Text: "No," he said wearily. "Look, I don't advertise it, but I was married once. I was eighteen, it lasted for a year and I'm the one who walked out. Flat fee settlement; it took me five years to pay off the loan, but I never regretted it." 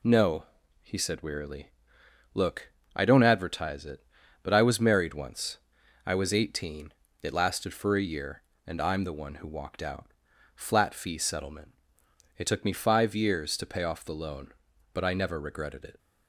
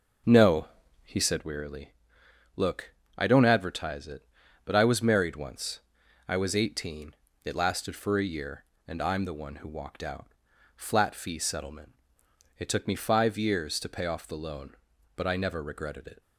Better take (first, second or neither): first